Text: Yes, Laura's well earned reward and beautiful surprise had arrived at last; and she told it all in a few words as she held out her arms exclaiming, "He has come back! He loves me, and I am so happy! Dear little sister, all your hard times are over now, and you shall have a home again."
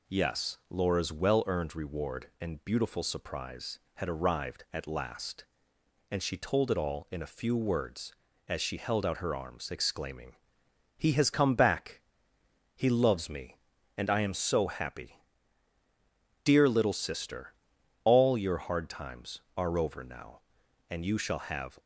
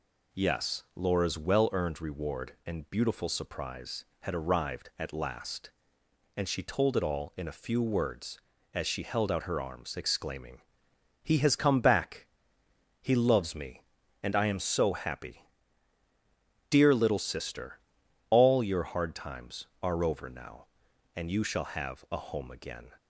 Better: second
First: stops before "a home again"; at 21.7 s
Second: none

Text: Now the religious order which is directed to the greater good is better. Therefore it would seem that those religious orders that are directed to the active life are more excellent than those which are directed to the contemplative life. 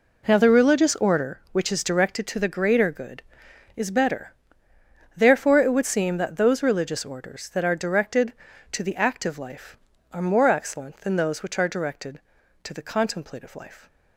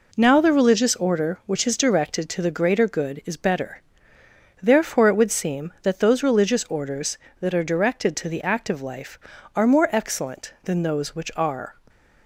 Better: first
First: none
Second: stops before "directed to the contemplative life"; at 11.8 s

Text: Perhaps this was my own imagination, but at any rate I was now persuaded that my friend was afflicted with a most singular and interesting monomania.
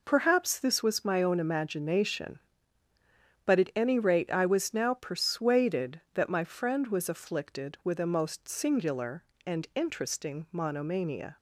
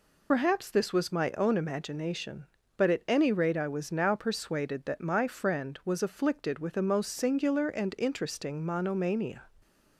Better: first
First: none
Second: loses the start of "Perhaps"; at 0.3 s; 55 ms

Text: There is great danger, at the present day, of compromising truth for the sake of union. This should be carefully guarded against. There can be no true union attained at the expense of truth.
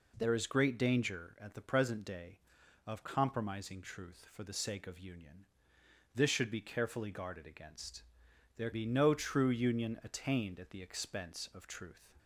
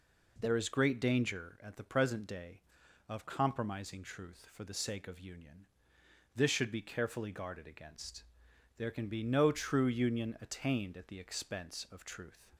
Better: second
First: skips "can"; at 8.7 s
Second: none

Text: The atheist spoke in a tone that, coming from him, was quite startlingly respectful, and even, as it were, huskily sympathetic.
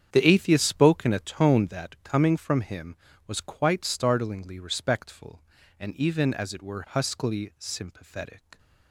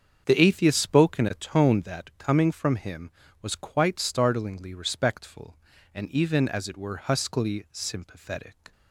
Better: second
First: gets quieter; strong; throughout; 13.5 dB // starts louder than the rest; strong; until 1.1 s; 8.5 dB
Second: starts louder than the rest; strong; until 1.2 s; 7 dB

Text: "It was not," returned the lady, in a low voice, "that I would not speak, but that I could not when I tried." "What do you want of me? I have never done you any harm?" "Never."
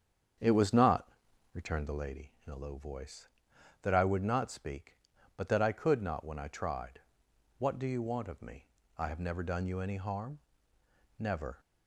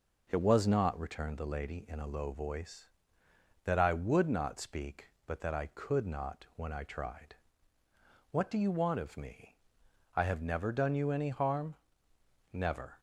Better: second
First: starts louder than the rest; strong; until 2.1 s; 7.5 dB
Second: none

